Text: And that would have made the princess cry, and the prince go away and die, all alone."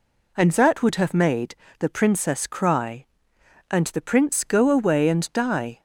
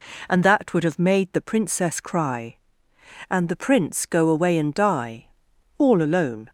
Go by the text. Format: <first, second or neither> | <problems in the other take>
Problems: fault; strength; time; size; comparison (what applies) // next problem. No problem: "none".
second | pauses between "made" and "the"; slight; at 1.5 s; 0.24 s long // stops before "all alone"; at 5.7 s